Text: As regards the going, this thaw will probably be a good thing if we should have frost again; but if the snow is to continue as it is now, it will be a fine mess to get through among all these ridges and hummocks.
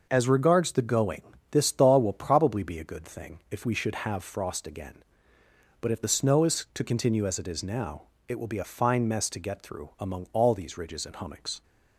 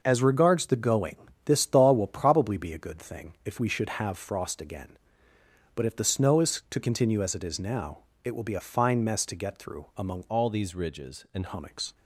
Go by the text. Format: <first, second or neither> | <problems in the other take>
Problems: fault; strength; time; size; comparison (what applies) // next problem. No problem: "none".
first | changes voice from "all" to "and"; from 10.3 to 11.4 s; 1.1 s long